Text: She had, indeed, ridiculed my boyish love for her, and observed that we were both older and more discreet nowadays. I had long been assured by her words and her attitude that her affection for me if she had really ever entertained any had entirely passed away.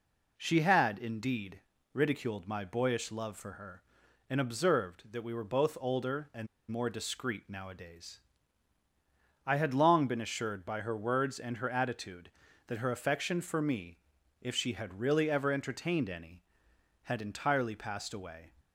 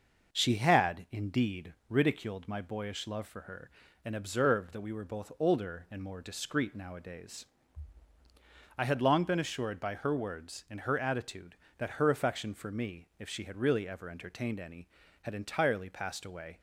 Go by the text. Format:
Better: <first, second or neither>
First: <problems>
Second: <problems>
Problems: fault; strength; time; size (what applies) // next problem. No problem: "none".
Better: second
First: pauses between "and" and "more"; slight; at 6.4 s; 0.24 s long // pauses between "me" and "if"; at 13.9 s; 0.44 s long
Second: none